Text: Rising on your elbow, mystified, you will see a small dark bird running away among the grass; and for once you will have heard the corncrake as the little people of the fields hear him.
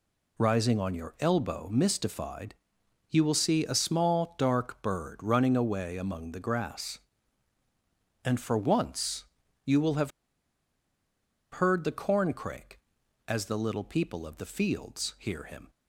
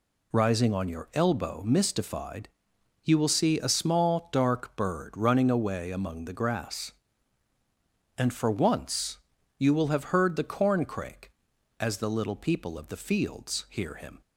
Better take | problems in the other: second | pauses between "once" and "you"; at 9.2 s; 0.40 s long; also in the second // pauses between "have" and "heard"; strong; at 10.1 s; 1.4 s long

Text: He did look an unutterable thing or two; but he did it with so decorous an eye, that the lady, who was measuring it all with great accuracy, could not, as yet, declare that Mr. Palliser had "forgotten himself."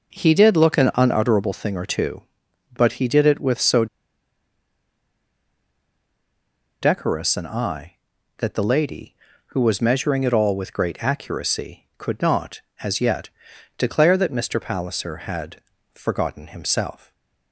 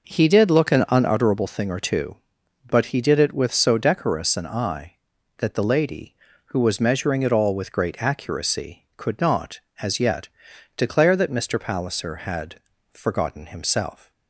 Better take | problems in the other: second | pauses between "so" and "decorous"; strong; at 3.8 s; 2.9 s long // pauses between "had" and "forgotten"; at 15.5 s; 0.38 s long; also in the second // stays silent after the last word; slight; from 16.9 s on; 0.6 s long

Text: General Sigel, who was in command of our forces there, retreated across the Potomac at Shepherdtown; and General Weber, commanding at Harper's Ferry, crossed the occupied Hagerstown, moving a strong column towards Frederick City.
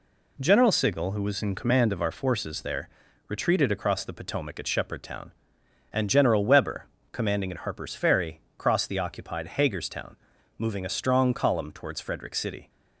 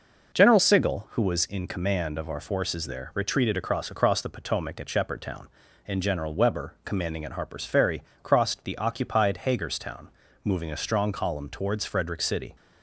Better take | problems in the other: first | says "across" twice; at 3.9 s

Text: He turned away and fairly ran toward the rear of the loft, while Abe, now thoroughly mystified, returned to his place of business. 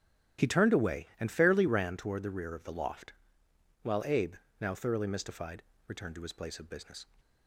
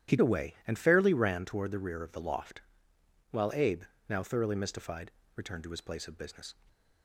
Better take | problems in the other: first | starts louder than the rest; strong; until 1.2 s; 11.5 dB; strong in the first // skips "turned"; at 0.1 s

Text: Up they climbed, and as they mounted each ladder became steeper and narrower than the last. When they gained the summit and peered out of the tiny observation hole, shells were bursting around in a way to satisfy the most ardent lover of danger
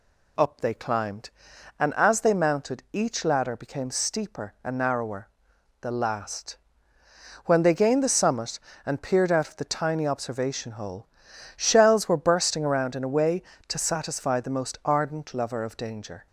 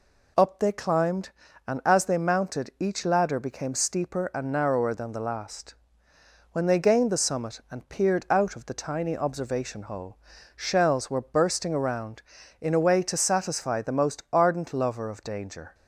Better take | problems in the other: second | skips "than"; at 5.5 s

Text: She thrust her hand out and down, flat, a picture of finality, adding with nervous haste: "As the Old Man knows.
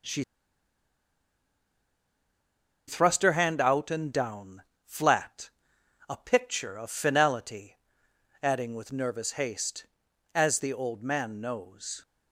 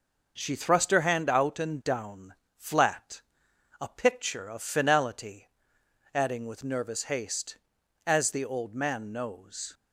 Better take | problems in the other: second | pauses between "She" and "thrust"; strong; at 0.2 s; 2.6 s long

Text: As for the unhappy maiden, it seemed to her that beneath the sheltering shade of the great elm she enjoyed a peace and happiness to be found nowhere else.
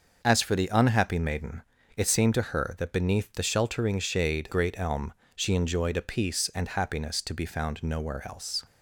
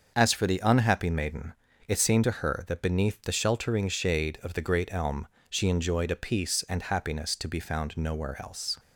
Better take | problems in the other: second | starts louder than the rest; until 1.2 s; 6.5 dB; also in the second // skips "of the"; at 4.5 s // pauses between "elm" and "she"; slight; at 5.1 s; 0.22 s long; slight in the second

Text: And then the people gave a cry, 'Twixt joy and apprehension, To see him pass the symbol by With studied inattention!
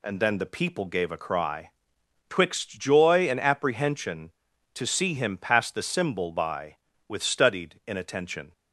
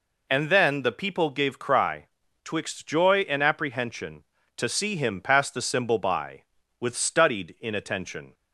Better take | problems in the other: first | skips "a"; at 1.5 s

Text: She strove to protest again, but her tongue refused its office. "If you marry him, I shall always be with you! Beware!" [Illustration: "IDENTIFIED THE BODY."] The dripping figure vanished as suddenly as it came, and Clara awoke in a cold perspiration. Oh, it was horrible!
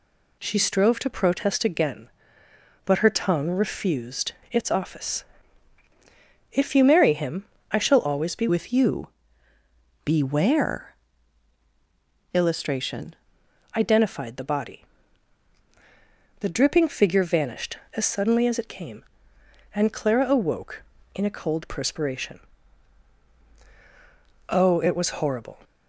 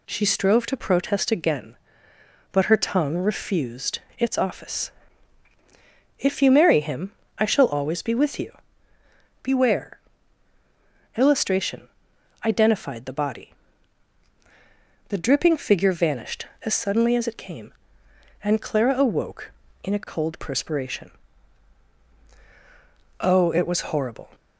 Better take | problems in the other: second | pauses between "refused" and "its"; slight; at 4.3 s; 0.22 s long; slight in the second // changes voice from "with" to "Illustration"; from 8.4 to 13.1 s; 4.7 s long

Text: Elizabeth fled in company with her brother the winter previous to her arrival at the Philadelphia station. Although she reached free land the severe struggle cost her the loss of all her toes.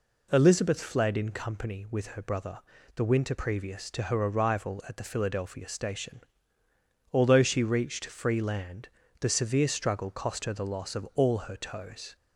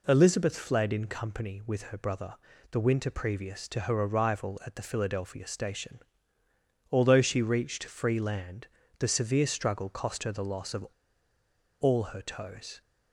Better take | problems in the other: first | pauses between "brother" and "the"; at 2.3 s; 0.38 s long; also in the first // pauses between "land" and "the"; slight; at 8.6 s; 0.32 s long; slight in the first // pauses between "of" and "all"; noticeable; at 10.8 s; 0.94 s long

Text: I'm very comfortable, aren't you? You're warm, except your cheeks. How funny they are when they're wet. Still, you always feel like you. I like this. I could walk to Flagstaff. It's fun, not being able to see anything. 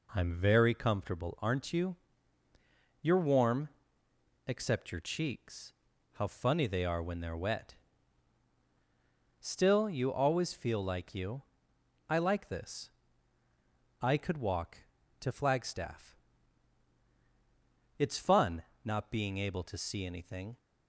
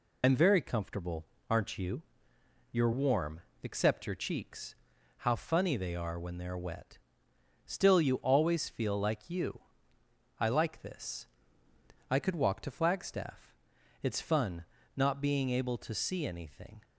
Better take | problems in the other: first | loses the start of "I'm"; at 0.2 s; 80 ms

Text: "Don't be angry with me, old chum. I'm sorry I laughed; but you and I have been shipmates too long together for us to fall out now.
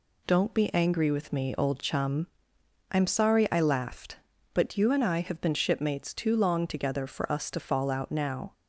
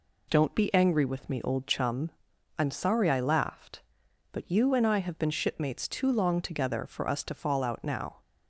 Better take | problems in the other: neither | none

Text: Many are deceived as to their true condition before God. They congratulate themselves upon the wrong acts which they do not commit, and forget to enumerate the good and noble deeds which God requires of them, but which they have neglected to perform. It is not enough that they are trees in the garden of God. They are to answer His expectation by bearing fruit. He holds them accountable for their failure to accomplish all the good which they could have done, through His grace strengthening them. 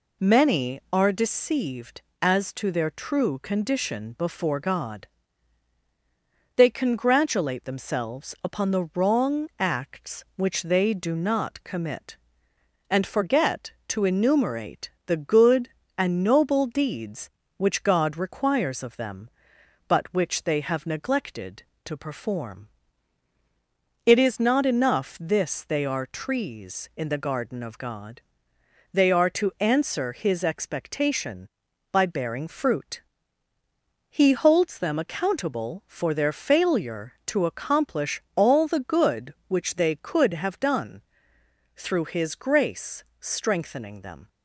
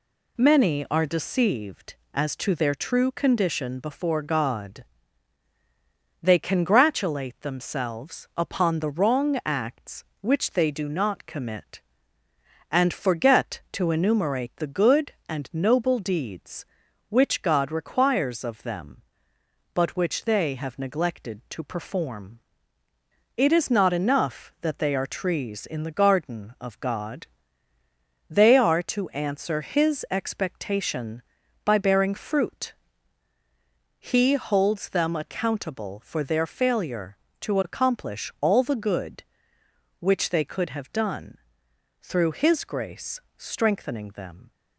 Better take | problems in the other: second | pauses between "enumerate" and "the"; slight; at 14.8 s; 0.16 s long // says "this" for "that"; at 25.2 s // pauses between "grace" and "strengthening"; slight; at 43.0 s; 0.16 s long; slight in the second

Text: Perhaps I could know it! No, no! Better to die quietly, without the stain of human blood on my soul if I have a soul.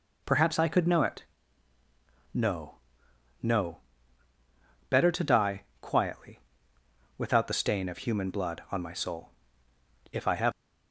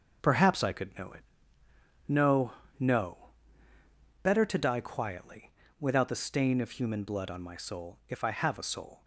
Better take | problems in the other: second | pauses between "die" and "quietly"; slight; at 5.6 s; 0.18 s long // pauses between "soul" and "if"; noticeable; at 9.3 s; 0.82 s long // stops before "a soul"; at 10.5 s

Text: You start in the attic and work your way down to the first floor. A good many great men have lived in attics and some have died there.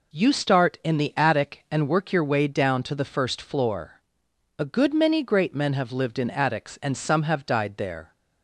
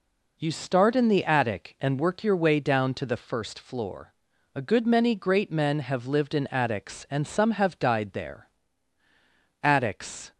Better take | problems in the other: first | goes on to say "Attics"; noticeable; from 9.6 s on; 0.68 s long

